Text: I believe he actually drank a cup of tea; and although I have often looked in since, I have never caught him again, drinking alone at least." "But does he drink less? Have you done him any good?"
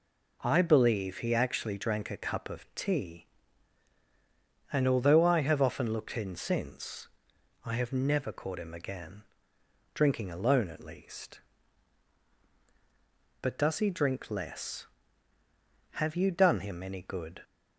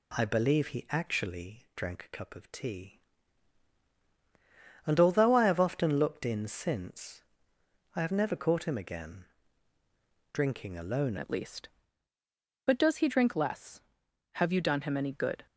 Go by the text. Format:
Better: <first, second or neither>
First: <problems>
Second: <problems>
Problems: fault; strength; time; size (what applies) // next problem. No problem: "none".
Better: first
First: none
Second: changes voice at "at"; from 11.1 s on; 4.3 s long